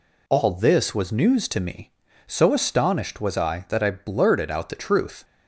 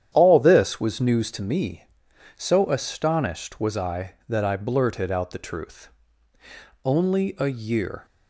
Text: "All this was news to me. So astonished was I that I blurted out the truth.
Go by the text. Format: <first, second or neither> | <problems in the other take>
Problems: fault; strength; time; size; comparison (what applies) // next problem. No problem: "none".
first | starts louder than the rest; strong; until 1.1 s; 9.5 dB // goes on to say "Only a year"; noticeable; from 6.8 s on; 1.2 s long